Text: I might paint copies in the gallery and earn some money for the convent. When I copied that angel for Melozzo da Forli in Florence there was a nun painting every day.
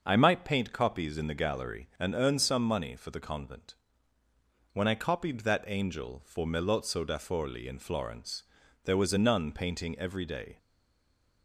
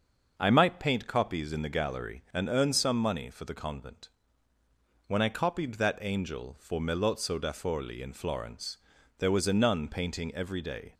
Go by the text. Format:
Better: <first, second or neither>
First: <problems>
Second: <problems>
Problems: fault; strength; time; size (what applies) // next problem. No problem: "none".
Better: second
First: starts louder than the rest; until 1.0 s; 6.5 dB // pauses between "Florence" and "there"; at 8.4 s; 0.42 s long // stays silent after the last word; slight; from 10.5 s on; 0.9 s long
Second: starts louder than the rest; until 1.3 s; 6.5 dB // pauses between "Florence" and "there"; at 8.7 s; 0.42 s long